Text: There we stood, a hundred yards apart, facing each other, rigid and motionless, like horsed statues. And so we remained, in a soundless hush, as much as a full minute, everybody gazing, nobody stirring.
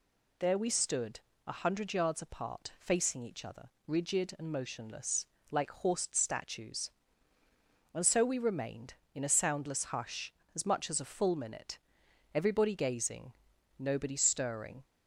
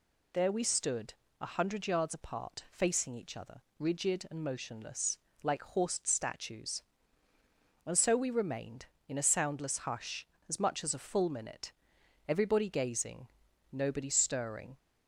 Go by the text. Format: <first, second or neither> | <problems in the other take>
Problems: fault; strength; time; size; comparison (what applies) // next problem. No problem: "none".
neither | none